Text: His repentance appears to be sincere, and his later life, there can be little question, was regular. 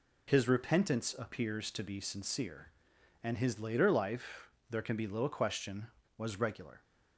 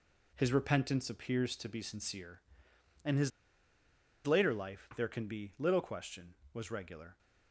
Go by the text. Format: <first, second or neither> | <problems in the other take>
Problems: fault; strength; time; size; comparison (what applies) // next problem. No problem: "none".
first | pauses between "his" and "later"; noticeable; at 3.3 s; 0.95 s long